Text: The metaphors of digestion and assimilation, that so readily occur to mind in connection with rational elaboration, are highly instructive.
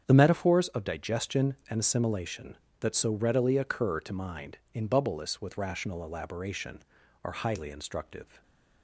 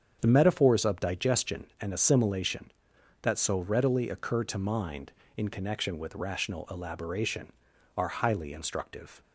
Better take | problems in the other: second | starts louder than the rest; strong; until 1.0 s; 8 dB; strong in the second // says "bubbleless" for "connection"; at 4.8 s

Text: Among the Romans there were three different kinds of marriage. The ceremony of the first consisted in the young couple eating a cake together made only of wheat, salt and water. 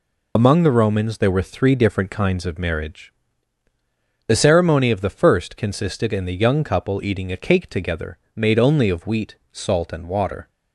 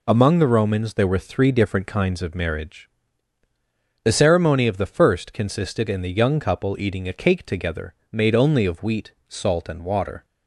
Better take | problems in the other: second | loses the start of "Among"; at 0.3 s; 35 ms // pauses between "together" and "made"; slight; at 8.1 s; 0.18 s long; slight in the second

